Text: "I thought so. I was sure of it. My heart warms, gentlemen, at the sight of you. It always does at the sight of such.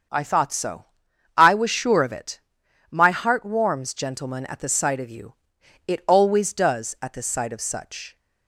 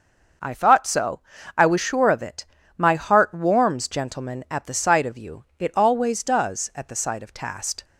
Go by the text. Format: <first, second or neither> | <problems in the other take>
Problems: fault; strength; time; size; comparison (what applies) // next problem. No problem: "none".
first | starts louder than the rest; noticeable; until 1.7 s; 6 dB; also in the first // says "tast" for "such"; at 7.3 s